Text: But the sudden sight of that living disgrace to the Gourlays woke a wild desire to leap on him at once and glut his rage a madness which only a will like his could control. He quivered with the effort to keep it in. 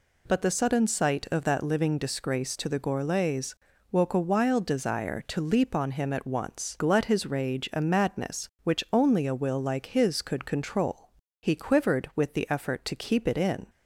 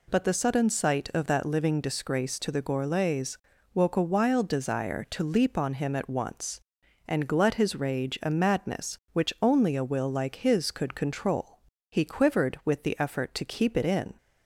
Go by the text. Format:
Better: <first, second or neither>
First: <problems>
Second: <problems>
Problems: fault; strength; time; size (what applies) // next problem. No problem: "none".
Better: second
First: pauses between "Gourlays" and "woke"; at 3.5 s; 0.38 s long // skips "and"; at 6.7 s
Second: pauses between "Gourlays" and "woke"; at 3.3 s; 0.38 s long